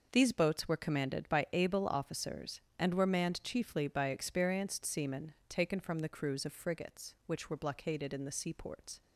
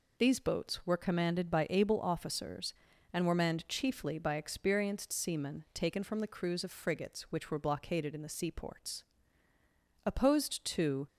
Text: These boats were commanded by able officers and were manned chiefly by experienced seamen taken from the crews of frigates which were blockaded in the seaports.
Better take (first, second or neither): first